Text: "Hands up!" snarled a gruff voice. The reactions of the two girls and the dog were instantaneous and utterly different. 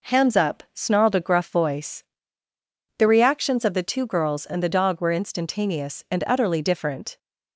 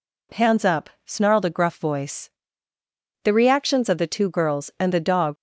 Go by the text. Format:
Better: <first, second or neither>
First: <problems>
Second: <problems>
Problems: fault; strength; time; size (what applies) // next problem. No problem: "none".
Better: first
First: none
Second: stops before "were instantaneous and utterly different"; at 5.3 s